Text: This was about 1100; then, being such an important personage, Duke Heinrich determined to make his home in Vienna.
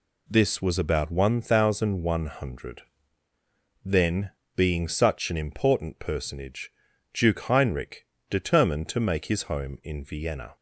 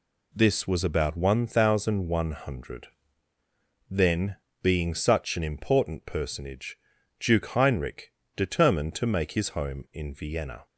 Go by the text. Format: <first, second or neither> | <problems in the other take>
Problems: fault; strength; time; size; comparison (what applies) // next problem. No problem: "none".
neither | pauses between "Heinrich" and "determined"; slight; the same in both